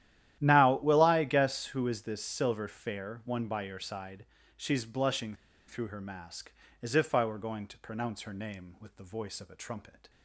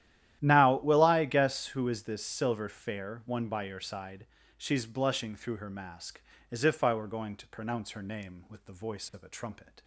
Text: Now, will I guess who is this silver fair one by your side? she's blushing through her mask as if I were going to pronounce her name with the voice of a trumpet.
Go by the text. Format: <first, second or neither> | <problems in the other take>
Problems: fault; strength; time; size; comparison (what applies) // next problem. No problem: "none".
second | starts louder than the rest; strong; until 1.4 s; 12.5 dB; strong in the second // pauses between "blushing" and "through"; slight; at 5.3 s; 0.32 s long